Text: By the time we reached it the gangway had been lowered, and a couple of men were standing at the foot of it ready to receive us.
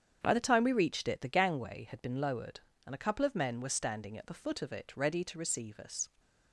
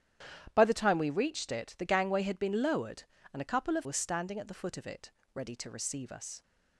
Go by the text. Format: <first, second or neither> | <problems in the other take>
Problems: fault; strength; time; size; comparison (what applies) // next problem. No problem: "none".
first | starts louder than the rest; strong; until 1.5 s; 11 dB; strong in the first // skips "men"; at 3.8 s // pauses between "it" and "ready"; slight; at 5.1 s; 0.24 s long